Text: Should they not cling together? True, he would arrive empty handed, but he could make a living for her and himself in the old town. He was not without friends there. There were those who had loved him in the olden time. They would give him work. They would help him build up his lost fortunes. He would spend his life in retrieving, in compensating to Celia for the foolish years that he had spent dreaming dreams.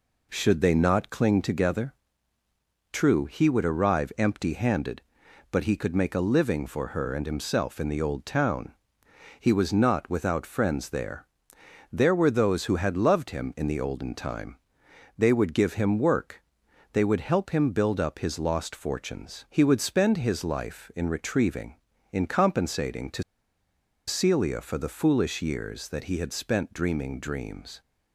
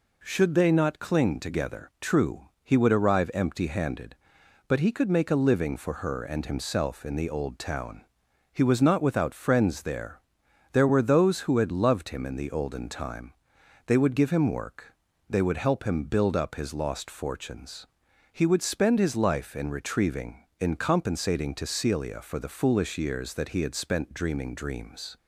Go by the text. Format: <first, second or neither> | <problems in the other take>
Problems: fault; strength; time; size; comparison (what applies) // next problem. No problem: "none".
second | pauses between "to" and "Celia"; noticeable; at 23.2 s; 0.85 s long